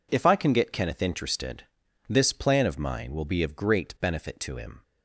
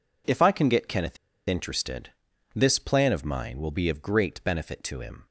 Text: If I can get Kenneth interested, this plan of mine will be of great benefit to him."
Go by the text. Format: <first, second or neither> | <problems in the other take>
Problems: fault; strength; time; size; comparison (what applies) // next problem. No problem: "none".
first | pauses between "Kenneth" and "interested"; slight; at 1.1 s; 0.33 s long